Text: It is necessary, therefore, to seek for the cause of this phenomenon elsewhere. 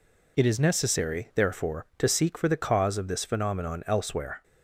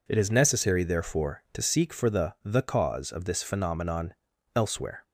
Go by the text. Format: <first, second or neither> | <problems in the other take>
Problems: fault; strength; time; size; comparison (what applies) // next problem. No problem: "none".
first | says "the" twice; at 2.4 s // pauses between "phenomenon" and "elsewhere"; at 4.1 s; 0.42 s long